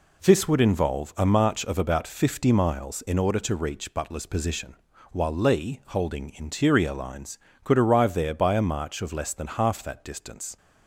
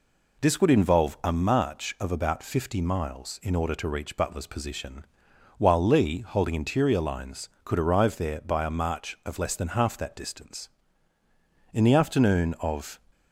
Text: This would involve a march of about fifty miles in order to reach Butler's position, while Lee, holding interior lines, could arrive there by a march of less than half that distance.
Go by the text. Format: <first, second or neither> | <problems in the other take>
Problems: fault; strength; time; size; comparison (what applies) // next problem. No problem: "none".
first | goes on to say "In the afternoon of"; noticeable; from 11.7 s on; 1.2 s long